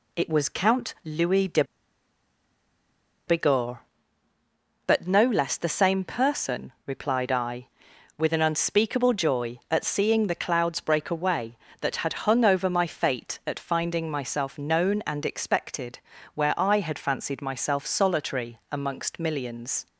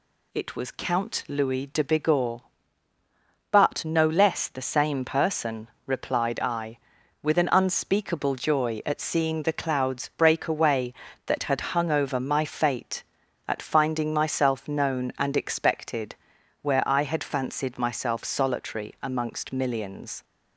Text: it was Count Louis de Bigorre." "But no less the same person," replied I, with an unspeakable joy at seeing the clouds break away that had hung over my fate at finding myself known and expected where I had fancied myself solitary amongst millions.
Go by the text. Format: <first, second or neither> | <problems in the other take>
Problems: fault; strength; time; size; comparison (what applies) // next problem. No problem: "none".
second | pauses between "de" and "Bigorre"; strong; at 1.6 s; 1.6 s long // pauses between "expected" and "where"; at 15.9 s; 0.38 s long; noticeable in the second